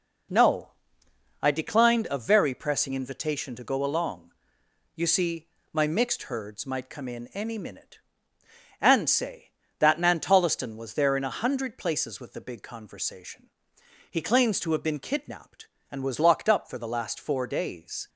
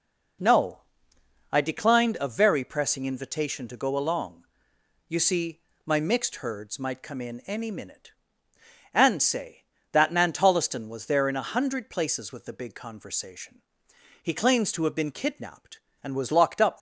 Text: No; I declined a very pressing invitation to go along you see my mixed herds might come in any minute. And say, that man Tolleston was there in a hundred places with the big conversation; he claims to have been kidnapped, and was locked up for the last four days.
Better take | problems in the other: first | pauses between "along" and "you"; noticeable; at 4.4 s; 0.64 s long; noticeable in the first // pauses between "see" and "my"; slight; at 5.5 s; 0.26 s long; slight in the first // stops before "for the last four days"; at 16.7 s

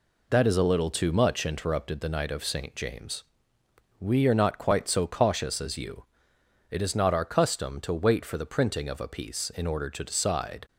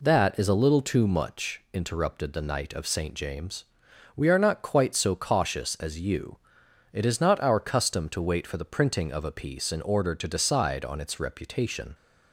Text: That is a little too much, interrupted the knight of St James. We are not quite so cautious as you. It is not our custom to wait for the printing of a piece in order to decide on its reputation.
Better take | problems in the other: second | stops before "on its reputation"; at 10.6 s

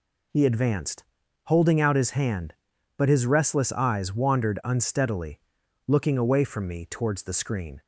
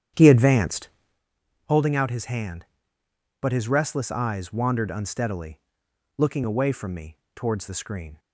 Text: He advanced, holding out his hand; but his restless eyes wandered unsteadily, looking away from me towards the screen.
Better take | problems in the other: first | starts louder than the rest; strong; until 1.2 s; 9.5 dB // pauses between "me" and "towards"; slight; at 7.1 s; 0.18 s long

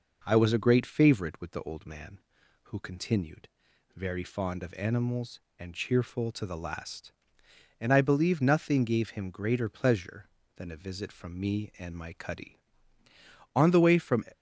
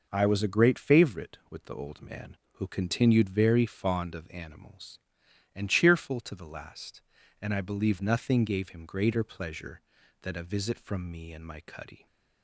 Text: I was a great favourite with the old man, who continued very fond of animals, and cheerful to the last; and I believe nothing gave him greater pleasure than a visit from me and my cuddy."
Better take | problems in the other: second | pauses between "continued" and "very"; noticeable; at 3.4 s; 0.46 s long // goes on to say "On the way from"; noticeable; from 13.5 s on; 0.68 s long

